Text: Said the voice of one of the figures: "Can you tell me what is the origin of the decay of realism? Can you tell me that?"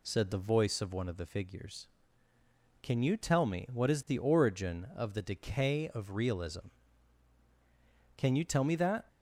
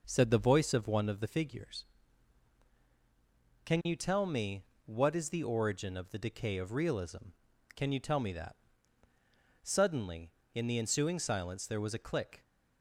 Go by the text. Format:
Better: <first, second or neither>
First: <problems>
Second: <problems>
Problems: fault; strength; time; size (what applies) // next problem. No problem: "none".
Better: first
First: none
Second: pauses between "me" and "what"; slight; at 4.6 s; 0.24 s long // goes on to say "Suddenly in the ensuing silence there was a click"; strong; from 9.6 s on; 2.8 s long